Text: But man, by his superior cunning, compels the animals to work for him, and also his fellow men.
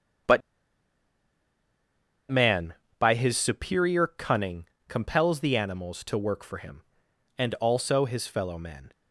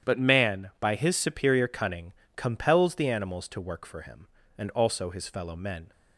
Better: second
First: starts louder than the rest; strong; until 3.4 s; 8.5 dB // pauses between "But" and "man"; strong; at 0.4 s; 1.9 s long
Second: starts louder than the rest; strong; until 1.1 s; 9.5 dB

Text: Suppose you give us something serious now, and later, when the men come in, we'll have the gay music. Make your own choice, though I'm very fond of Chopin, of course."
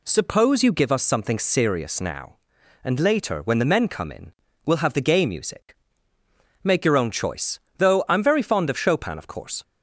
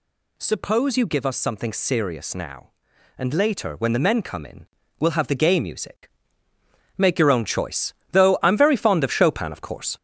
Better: first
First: none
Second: gets louder; noticeable; throughout; 4 dB

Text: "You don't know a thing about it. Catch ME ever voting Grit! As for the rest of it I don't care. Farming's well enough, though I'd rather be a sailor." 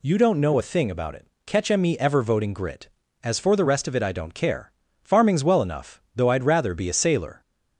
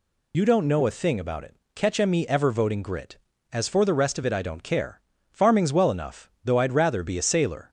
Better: first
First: none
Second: loses the start of "You"; at 0.3 s; 55 ms

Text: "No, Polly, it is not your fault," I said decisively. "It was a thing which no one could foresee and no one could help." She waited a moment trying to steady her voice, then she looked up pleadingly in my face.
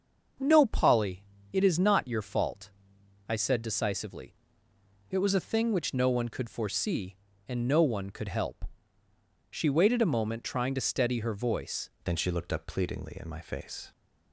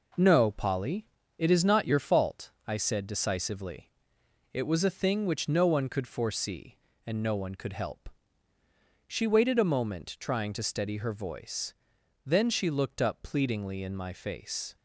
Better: second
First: starts louder than the rest; until 1.6 s; 6.5 dB // changes voice at "then"; from 12.0 s on; 1.9 s long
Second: none

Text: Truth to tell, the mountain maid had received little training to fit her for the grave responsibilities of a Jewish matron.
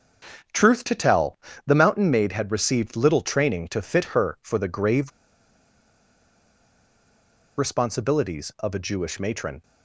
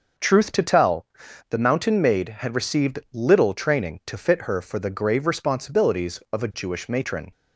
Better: second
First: starts louder than the rest; until 1.8 s; 7 dB // pauses between "grave" and "responsibilities"; strong; at 5.1 s; 2.4 s long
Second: starts louder than the rest; noticeable; until 1.6 s; 6 dB

